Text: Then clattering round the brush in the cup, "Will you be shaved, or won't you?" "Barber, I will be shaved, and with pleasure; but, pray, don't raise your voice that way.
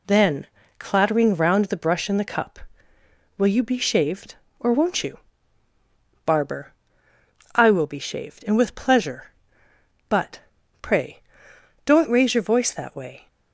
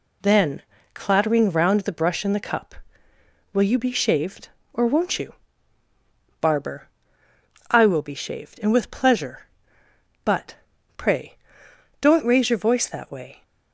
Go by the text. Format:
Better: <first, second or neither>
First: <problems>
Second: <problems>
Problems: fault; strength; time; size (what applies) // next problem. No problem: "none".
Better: neither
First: pauses between "Then" and "clattering"; slight; at 0.4 s; 0.32 s long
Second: pauses between "Then" and "clattering"; slight; at 0.6 s; 0.32 s long